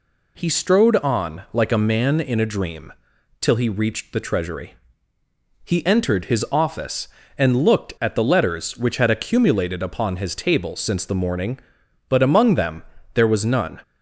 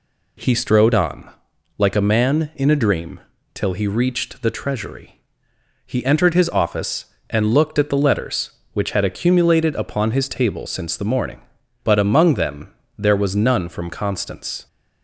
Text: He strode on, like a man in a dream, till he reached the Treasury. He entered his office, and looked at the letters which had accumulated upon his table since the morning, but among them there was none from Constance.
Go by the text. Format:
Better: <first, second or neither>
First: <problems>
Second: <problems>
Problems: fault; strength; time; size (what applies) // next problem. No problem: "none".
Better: second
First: pauses between "them" and "there"; slight; at 12.8 s; 0.32 s long // stops before "from Constance"; at 13.8 s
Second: pauses between "them" and "there"; slight; at 12.7 s; 0.28 s long